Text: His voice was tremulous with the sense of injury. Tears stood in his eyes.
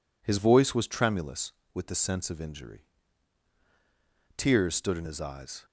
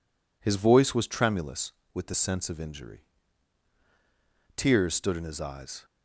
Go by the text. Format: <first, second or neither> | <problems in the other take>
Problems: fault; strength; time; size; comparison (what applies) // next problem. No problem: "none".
neither | none